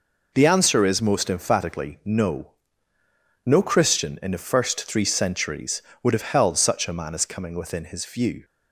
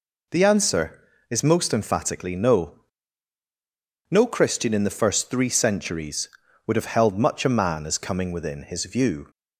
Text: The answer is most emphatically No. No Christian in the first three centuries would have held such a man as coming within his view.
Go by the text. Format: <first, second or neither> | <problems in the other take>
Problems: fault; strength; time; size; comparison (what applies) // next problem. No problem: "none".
first | says "much" for "such"; at 7.1 s